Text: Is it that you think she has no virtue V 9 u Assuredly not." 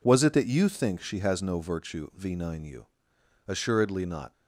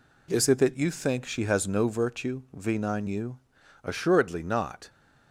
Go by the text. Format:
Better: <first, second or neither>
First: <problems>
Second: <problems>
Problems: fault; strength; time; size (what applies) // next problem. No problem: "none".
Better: second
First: says "Was" for "Is"; at 0.0 s // pauses between "u" and "Assuredly"; noticeable; at 2.8 s; 0.60 s long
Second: pauses between "u" and "Assuredly"; at 3.3 s; 0.44 s long